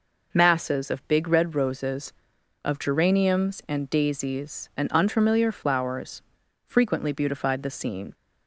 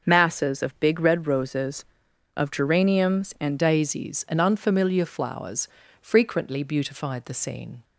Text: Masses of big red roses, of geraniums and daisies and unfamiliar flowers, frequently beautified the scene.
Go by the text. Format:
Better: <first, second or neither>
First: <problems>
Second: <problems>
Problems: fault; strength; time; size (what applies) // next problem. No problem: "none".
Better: first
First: none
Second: changes voice at "daisies"; from 3.5 s on; 4.3 s long